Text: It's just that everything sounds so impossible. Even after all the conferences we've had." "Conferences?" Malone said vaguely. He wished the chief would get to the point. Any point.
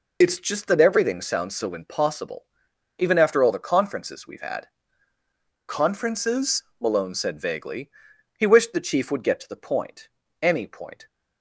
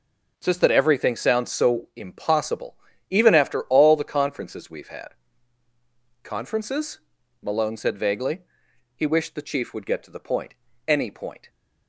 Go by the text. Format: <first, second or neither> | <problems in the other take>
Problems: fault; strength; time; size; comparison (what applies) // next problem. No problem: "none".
second | loses the start of "It's"; at 0.2 s; 35 ms